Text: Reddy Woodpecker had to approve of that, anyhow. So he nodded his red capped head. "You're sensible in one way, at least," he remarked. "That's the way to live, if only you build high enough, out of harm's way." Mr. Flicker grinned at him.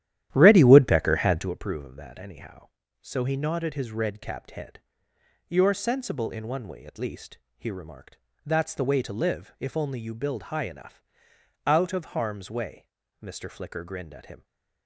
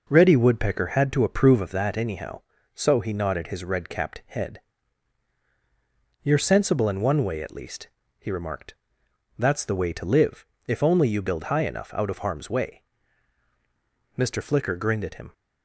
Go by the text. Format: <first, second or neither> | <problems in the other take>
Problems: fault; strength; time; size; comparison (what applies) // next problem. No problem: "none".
second | starts louder than the rest; strong; until 1.5 s; 12 dB // stays silent after the last word; slight; from 14.3 s on; 0.5 s long